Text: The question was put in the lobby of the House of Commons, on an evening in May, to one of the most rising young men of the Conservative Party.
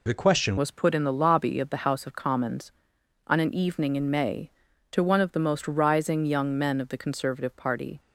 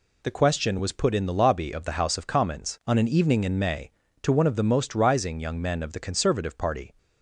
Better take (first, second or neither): second